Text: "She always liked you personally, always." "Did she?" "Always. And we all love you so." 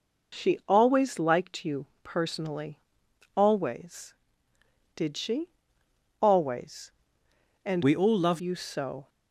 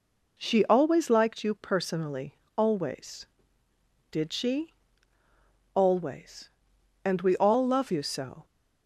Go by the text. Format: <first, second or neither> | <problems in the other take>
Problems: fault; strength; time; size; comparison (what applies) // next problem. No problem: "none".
second | pauses between "you" and "personally"; slight; at 1.8 s; 0.16 s long // changes voice from "we" to "love"; from 7.8 to 8.4 s; 0.6 s long